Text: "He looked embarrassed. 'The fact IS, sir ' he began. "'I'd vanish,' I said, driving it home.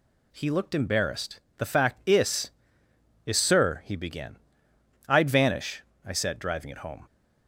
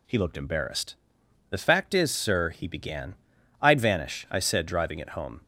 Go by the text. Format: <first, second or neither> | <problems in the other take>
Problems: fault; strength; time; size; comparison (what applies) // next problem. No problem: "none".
second | says "IS" twice; at 3.2 s